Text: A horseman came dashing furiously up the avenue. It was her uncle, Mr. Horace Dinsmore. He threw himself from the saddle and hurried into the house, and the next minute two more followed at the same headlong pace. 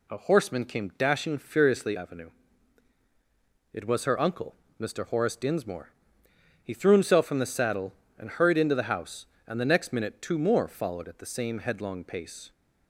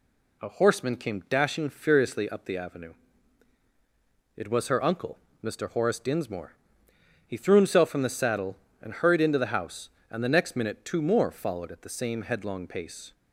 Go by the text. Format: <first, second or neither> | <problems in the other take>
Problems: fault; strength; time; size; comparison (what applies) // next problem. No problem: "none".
second | skips "up the"; at 1.9 s